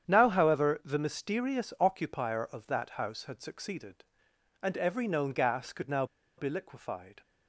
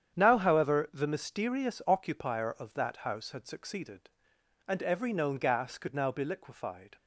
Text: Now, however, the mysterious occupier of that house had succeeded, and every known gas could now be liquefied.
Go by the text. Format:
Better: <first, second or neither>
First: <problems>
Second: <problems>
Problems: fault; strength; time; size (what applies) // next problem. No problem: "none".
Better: second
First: starts louder than the rest; strong; until 1.1 s; 9 dB // pauses between "now" and "be"; slight; at 6.0 s; 0.33 s long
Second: starts louder than the rest; strong; until 1.2 s; 9 dB